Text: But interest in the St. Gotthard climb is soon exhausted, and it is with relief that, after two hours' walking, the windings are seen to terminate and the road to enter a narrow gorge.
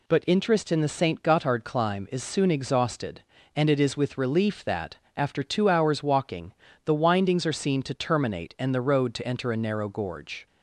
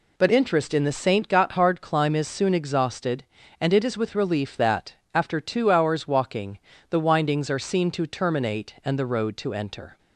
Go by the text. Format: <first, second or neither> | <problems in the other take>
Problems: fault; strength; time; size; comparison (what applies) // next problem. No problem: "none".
first | stops before "a narrow gorge"; at 9.9 s